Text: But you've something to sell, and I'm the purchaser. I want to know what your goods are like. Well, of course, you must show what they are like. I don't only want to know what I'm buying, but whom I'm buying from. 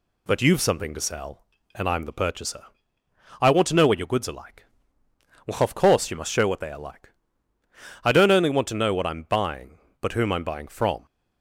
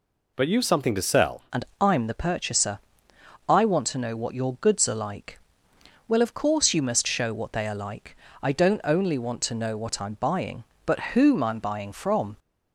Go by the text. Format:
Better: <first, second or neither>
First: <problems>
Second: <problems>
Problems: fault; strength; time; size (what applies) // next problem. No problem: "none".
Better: first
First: none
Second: changes voice at "and"; from 1.5 s on; 10.8 s long // pauses between "and" and "I'm"; slight; at 1.6 s; 0.16 s long // pauses between "but" and "whom"; slight; at 10.9 s; 0.16 s long